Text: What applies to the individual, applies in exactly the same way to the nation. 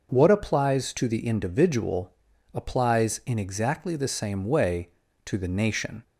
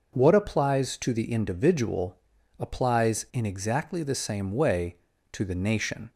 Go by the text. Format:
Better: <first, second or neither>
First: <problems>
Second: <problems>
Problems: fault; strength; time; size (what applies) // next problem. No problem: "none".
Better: neither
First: none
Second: none